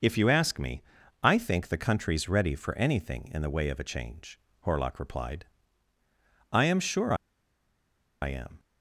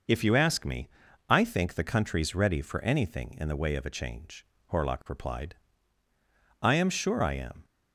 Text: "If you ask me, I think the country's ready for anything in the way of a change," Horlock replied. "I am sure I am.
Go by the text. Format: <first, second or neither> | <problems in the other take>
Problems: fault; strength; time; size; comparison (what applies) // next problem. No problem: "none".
second | pauses between "sure" and "I"; at 7.1 s; 1.0 s long